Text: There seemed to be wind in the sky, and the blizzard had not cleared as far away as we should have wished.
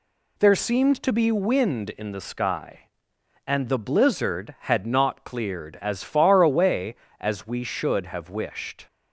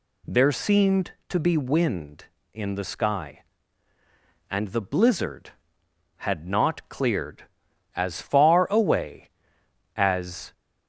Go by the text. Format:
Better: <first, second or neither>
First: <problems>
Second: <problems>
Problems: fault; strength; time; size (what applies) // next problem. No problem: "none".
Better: first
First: none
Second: stops before "we should have wished"; at 10.5 s